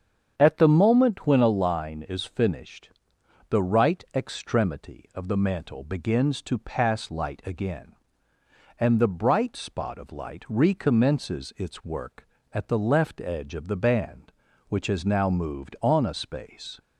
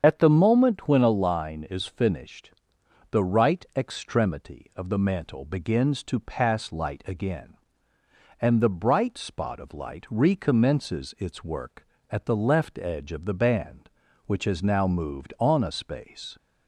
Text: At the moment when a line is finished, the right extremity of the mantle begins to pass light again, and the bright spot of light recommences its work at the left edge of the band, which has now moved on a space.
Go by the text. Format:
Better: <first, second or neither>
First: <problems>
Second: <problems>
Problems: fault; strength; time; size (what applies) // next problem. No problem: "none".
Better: first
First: starts louder than the rest; strong; until 1.3 s; 7.5 dB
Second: loses the start of "At"; at 0.0 s; 45 ms // starts louder than the rest; strong; until 1.0 s; 7.5 dB